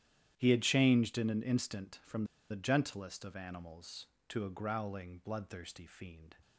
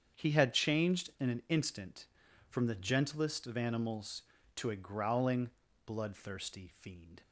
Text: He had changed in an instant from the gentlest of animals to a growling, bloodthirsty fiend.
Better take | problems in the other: second | starts louder than the rest; strong; until 1.3 s; 11 dB; strong in the second // pauses between "from" and "the"; slight; at 2.2 s; 0.25 s long

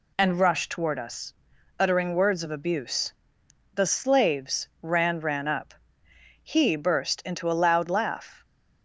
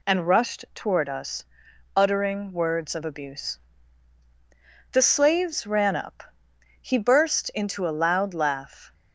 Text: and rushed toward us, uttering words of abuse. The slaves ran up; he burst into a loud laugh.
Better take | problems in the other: second | says "ran" twice; at 5.2 s

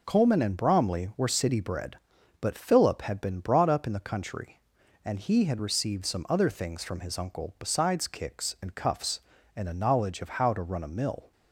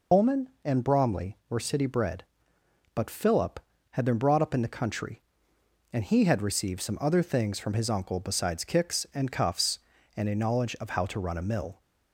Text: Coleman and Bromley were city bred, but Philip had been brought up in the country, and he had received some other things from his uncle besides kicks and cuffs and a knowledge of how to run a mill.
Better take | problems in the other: first | loses the start of "Coleman"; at 0.1 s; 95 ms

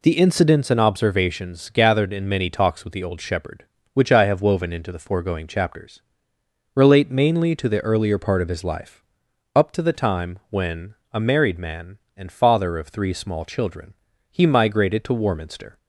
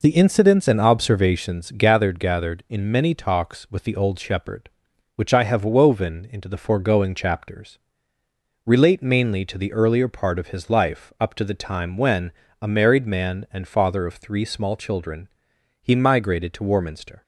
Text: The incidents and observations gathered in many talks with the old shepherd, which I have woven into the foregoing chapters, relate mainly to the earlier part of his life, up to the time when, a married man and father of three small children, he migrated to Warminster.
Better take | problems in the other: first | says "gathered" twice; at 2.1 s

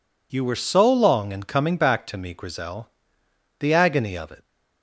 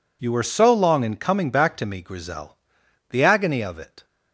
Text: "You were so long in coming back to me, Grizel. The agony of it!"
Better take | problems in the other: neither | none

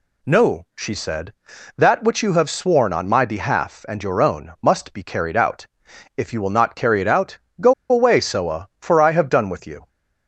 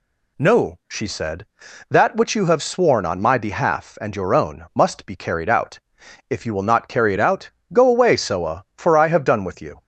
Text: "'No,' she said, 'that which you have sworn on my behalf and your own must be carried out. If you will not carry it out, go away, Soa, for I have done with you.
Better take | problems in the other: second | pauses between "go" and "away"; slight; at 7.7 s; 0.16 s long

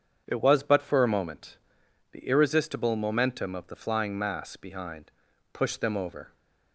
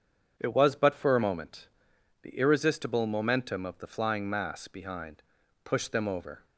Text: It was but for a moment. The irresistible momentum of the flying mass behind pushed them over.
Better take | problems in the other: neither | starts louder than the rest; strong; the same in both // pauses between "behind" and "pushed"; the same in both

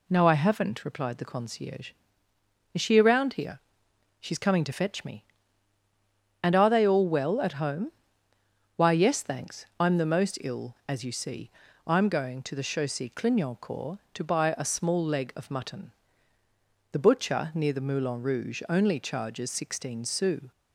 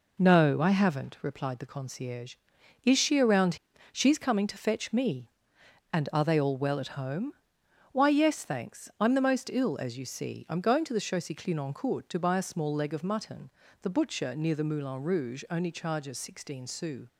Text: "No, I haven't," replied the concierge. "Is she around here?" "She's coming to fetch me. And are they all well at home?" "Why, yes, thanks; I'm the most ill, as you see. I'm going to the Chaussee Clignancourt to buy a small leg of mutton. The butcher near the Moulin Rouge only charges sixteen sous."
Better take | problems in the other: first | skips "here"; at 3.7 s

